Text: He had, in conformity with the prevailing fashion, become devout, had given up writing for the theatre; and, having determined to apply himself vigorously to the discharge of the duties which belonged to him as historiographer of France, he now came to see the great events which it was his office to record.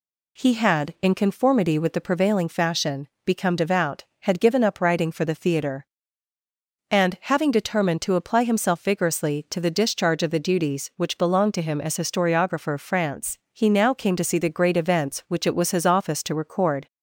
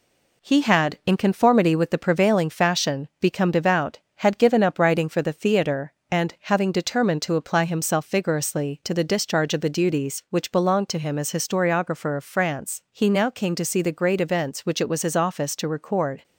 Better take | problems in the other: first | gets quieter; slight; throughout; 2.5 dB

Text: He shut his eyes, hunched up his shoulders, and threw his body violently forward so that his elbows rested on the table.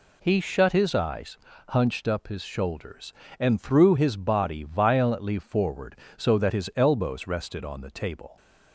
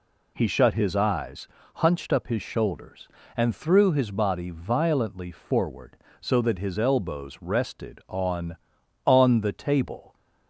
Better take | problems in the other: first | says "on" twice; at 9.0 s

